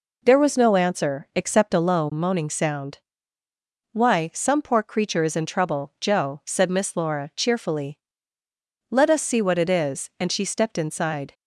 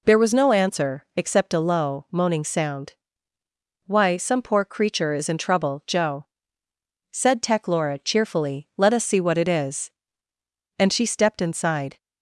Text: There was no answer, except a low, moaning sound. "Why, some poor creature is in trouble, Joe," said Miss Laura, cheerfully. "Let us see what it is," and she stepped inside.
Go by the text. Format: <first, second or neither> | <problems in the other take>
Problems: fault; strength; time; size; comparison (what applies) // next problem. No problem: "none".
first | says "Tech" for "Miss"; at 7.3 s